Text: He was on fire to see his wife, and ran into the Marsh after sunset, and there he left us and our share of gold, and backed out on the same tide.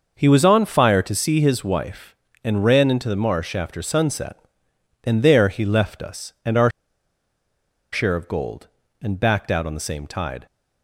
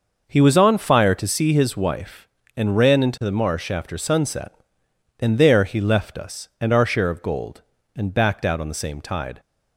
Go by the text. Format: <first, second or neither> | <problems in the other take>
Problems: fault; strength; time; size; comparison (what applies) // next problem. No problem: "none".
second | pauses between "our" and "share"; at 6.7 s; 1.2 s long